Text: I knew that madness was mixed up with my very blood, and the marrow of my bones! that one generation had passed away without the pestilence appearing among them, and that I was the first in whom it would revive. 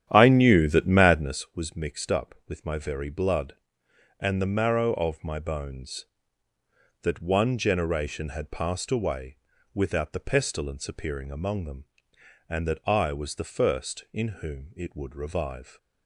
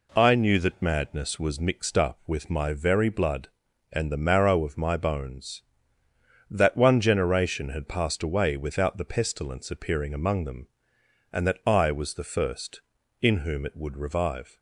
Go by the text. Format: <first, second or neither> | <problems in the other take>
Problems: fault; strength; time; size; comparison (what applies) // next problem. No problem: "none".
second | starts louder than the rest; strong; until 1.5 s; 10.5 dB // pauses between "away" and "without"; at 9.3 s; 0.38 s long